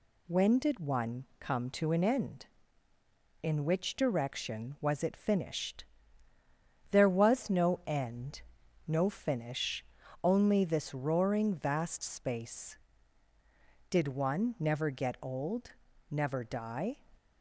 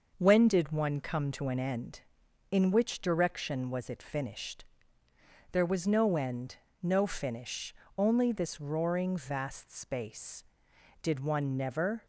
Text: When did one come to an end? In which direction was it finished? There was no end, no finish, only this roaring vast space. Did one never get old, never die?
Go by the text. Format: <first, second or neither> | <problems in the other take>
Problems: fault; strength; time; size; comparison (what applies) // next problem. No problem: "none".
first | starts louder than the rest; noticeable; until 1.1 s; 6 dB // stops before "get old never die"; at 12.0 s